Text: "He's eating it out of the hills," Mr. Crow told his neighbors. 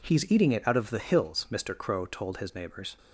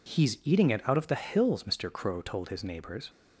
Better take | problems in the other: neither | none

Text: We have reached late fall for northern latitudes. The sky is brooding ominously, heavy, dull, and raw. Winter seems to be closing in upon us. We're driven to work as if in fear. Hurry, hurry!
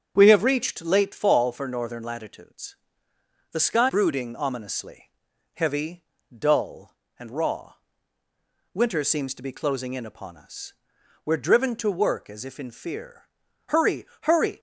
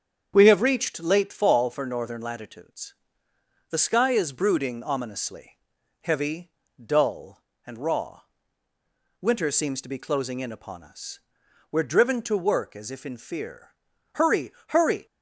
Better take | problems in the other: second | starts louder than the rest; strong; until 1.1 s; 7.5 dB; strong in the second // skips "is"; at 3.8 s

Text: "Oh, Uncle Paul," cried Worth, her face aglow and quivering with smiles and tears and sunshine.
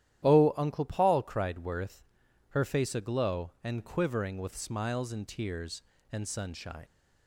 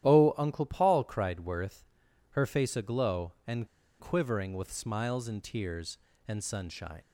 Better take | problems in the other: first | starts louder than the rest; strong; until 1.0 s; 11.5 dB; strong in the first // pauses between "and" and "quivering"; slight; at 3.6 s; 0.33 s long

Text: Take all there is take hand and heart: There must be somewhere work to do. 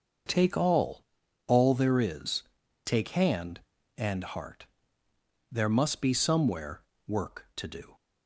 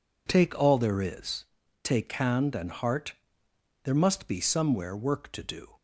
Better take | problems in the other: second | starts louder than the rest; noticeable; until 1.7 s; 6 dB // says "all" twice; at 1.4 s // pauses between "is" and "take"; at 2.4 s; 0.42 s long; also in the second // pauses between "somewhere" and "work"; slight; at 6.8 s; 0.26 s long

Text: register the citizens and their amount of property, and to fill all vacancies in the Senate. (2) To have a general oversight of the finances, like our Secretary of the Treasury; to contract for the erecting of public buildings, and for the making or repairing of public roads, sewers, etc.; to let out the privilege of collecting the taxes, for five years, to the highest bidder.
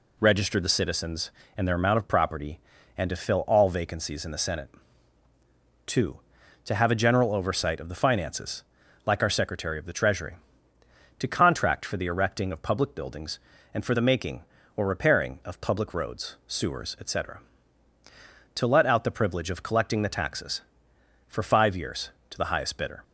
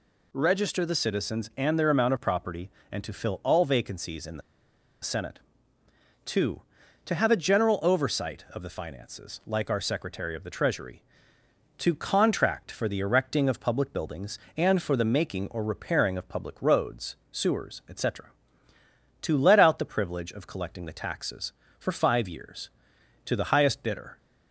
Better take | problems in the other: first | pauses between "the" and "Senate"; noticeable; at 4.4 s; 0.61 s long

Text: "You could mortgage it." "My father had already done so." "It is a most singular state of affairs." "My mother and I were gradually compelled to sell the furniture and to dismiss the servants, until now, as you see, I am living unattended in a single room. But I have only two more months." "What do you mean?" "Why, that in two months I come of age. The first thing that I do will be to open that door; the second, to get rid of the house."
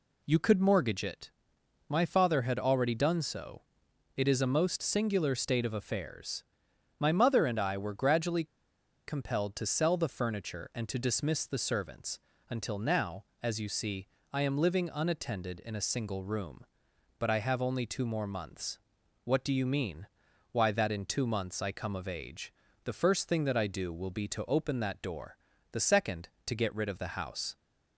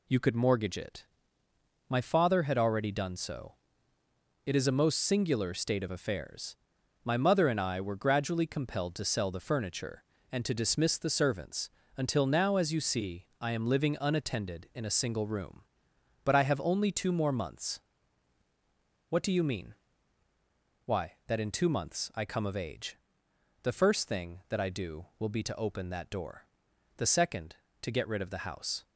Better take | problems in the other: second | pauses between "gradually" and "compelled"; noticeable; at 8.4 s; 0.62 s long

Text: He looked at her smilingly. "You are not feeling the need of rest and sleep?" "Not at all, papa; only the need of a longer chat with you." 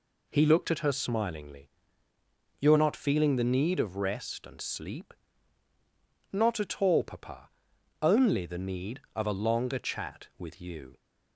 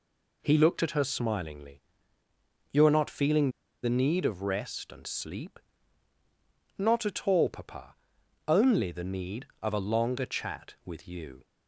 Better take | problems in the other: first | pauses between "feeling" and "the"; slight; at 3.4 s; 0.33 s long

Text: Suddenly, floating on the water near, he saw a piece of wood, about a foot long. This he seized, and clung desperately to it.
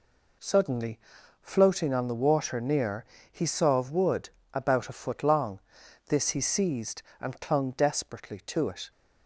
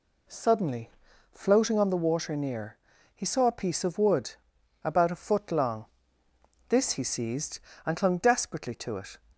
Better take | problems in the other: second | skips "a piece"; at 3.7 s

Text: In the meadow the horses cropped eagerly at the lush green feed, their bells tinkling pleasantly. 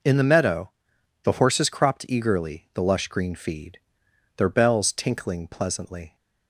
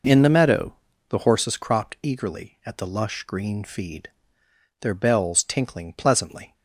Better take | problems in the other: second | pauses between "meadow" and "the"; noticeable; at 0.7 s; 0.52 s long; slight in the second // skips "at"; at 2.6 s

